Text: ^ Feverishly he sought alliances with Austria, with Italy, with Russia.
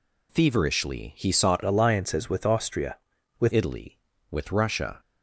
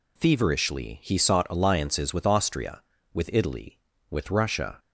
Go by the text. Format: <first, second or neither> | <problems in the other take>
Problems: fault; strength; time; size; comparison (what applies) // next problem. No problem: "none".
second | changes voice from "alliances" to "with"; from 1.6 to 3.5 s; 1.9 s long